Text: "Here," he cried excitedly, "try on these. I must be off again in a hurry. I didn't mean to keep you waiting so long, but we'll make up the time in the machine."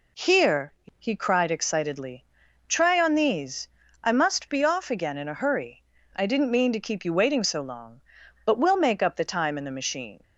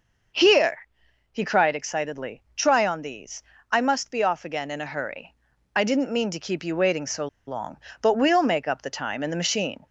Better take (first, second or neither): first